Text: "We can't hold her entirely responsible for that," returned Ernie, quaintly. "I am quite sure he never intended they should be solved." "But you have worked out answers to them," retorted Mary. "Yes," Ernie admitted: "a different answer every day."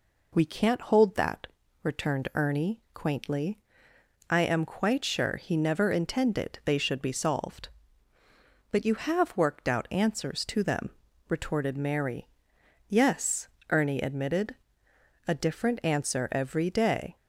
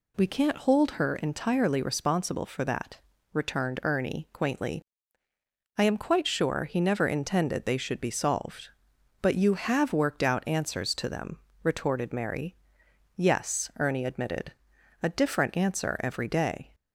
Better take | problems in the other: second | skips "her entirely responsible for"; at 1.1 s

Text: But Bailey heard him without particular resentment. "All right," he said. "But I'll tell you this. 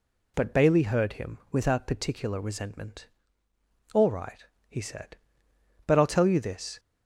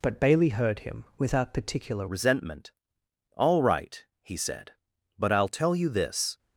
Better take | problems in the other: first | pauses between "him" and "without"; slight; at 1.0 s; 0.16 s long; slight in the first // changes voice at "resentment"; from 2.0 s on; 4.3 s long

